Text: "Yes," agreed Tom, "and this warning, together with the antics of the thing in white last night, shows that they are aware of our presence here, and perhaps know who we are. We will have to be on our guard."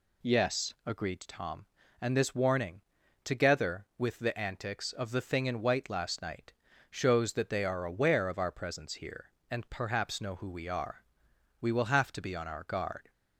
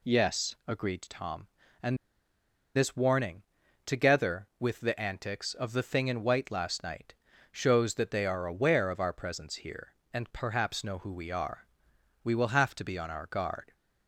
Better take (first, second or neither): first